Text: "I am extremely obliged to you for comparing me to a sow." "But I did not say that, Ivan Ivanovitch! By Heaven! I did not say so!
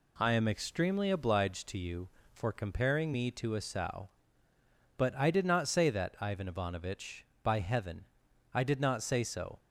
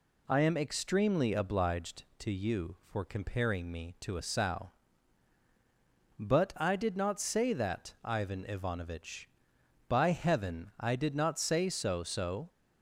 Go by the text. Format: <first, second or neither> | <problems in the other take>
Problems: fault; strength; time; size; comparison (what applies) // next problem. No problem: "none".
first | says "so" twice; at 12.0 s